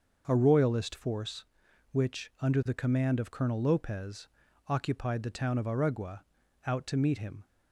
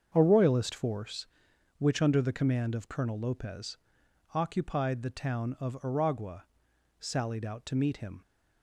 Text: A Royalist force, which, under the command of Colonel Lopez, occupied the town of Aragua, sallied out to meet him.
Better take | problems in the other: second | starts louder than the rest; noticeable; until 1.2 s; 6 dB; also in the second // skips "sallied"; at 6.4 s

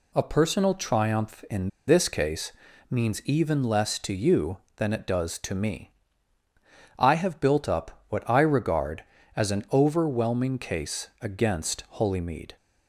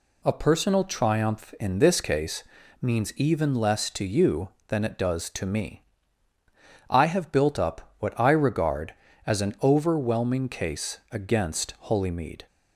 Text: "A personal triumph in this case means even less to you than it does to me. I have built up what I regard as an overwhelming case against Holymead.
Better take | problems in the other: second | pauses between "in" and "this"; slight; at 1.6 s; 0.19 s long // pauses between "case" and "means"; at 2.5 s; 0.38 s long; also in the second

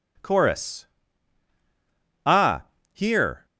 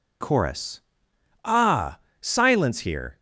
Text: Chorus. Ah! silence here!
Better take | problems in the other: second | skips "silence"; at 2.7 s

